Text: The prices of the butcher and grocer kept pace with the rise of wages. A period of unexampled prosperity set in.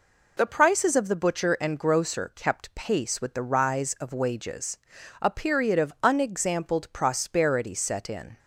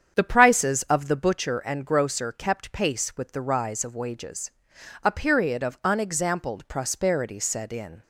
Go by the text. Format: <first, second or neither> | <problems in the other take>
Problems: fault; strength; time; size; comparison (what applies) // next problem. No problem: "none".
first | starts louder than the rest; strong; until 1.4 s; 8 dB